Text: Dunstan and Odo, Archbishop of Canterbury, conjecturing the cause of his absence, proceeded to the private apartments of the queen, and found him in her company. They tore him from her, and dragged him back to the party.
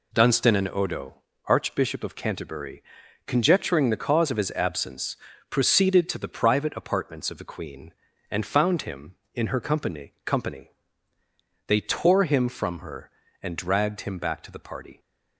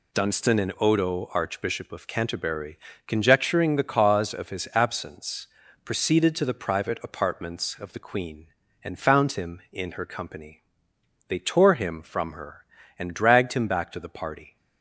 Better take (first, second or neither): second